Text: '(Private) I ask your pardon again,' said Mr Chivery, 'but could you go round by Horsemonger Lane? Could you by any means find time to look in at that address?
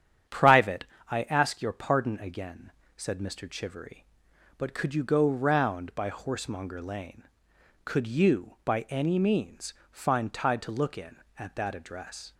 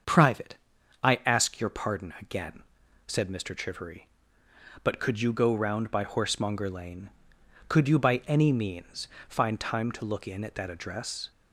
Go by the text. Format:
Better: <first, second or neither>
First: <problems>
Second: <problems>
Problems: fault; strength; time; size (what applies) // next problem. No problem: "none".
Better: second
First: starts louder than the rest; strong; until 1.5 s; 9 dB // pauses between "means" and "find"; slight; at 9.7 s; 0.18 s long // says "tide" for "time"; at 10.3 s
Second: starts louder than the rest; until 1.5 s; 7 dB // pauses between "means" and "find"; slight; at 9.0 s; 0.22 s long